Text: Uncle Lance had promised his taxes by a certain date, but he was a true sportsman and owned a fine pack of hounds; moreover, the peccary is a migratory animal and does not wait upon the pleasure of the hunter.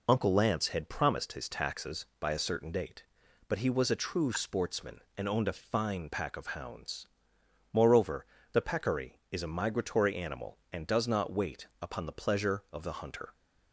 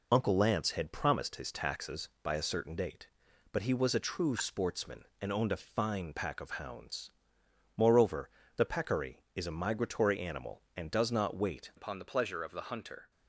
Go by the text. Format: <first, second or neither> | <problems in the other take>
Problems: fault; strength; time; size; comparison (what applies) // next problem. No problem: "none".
first | changes voice at "upon"; from 11.7 s on; 1.4 s long